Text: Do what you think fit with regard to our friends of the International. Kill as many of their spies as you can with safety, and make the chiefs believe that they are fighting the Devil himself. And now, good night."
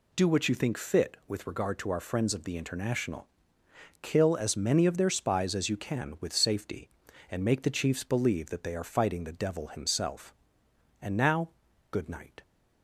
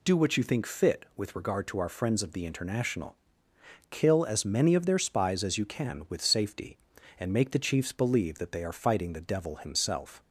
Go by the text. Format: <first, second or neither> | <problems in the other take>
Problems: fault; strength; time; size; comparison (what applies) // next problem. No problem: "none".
first | stops before "And now good night"; at 10.2 s